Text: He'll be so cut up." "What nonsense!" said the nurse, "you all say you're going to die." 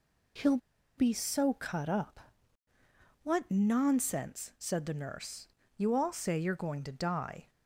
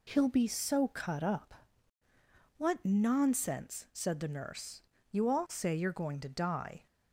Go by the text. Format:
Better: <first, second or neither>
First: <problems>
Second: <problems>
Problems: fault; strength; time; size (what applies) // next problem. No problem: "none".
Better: second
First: pauses between "He'll" and "be"; at 0.5 s; 0.38 s long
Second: none